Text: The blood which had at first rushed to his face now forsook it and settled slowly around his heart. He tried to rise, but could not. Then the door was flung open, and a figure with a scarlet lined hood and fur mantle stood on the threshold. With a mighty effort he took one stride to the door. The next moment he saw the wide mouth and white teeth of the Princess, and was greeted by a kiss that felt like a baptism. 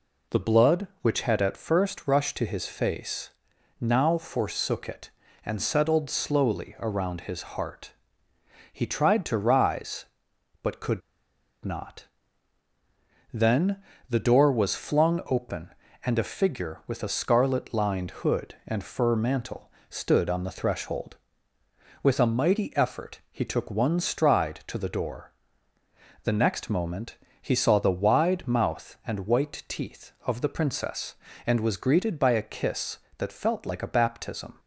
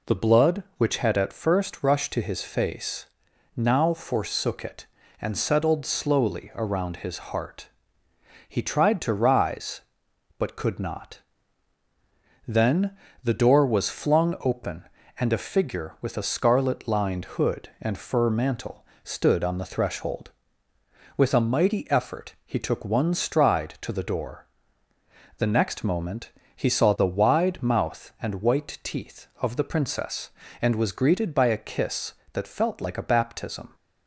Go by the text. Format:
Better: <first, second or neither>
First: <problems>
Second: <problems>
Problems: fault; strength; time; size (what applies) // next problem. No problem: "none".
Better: second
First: pauses between "face" and "now"; noticeable; at 3.2 s; 0.50 s long // pauses between "could" and "not"; noticeable; at 11.0 s; 0.64 s long // pauses between "Then" and "the"; slight; at 13.8 s; 0.26 s long // pauses between "mantle" and "stood"; slight; at 19.6 s; 0.20 s long // pauses between "moment" and "he"; slight; at 27.1 s; 0.24 s long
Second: pauses between "face" and "now"; noticeable; at 3.0 s; 0.50 s long // pauses between "Then" and "the"; slight; at 12.9 s; 0.26 s long // pauses between "mantle" and "stood"; slight; at 18.8 s; 0.20 s long // pauses between "moment" and "he"; slight; at 26.3 s; 0.24 s long